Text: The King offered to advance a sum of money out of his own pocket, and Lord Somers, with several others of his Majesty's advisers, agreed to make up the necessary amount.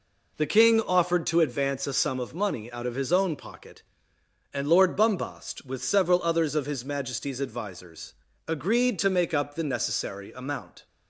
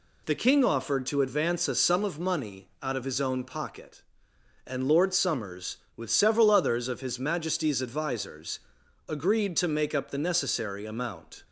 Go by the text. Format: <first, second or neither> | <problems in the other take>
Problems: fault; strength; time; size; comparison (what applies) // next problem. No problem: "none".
second | says "Bumbast" for "Somers"; at 4.9 s